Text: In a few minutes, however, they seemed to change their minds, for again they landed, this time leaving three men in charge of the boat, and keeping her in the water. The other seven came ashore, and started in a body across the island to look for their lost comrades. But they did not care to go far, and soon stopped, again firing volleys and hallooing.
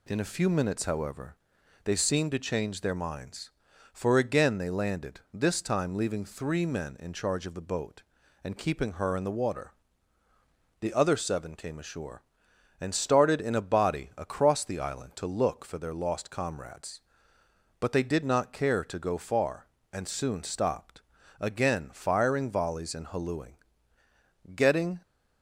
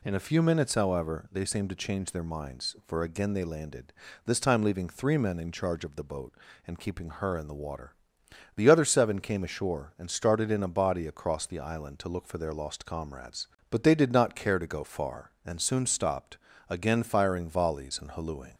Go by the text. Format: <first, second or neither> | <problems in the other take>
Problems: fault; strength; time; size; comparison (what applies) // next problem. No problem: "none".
second | goes on to say "Getting"; slight; from 24.5 s on; 0.46 s long